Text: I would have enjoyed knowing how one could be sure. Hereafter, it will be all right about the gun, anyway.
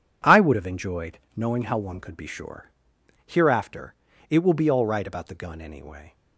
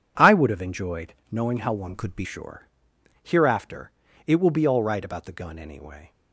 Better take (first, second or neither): first